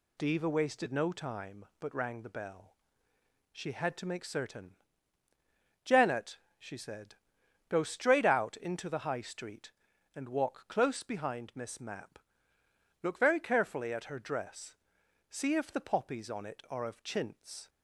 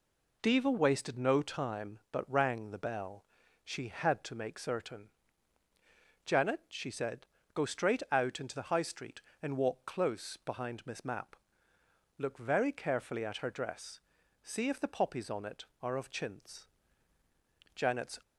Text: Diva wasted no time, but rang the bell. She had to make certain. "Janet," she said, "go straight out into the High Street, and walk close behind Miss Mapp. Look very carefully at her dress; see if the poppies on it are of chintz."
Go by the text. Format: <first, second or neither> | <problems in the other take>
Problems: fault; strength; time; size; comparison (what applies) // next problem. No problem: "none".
first | goes on to say "Janet's"; slight; from 17.7 s on; 0.44 s long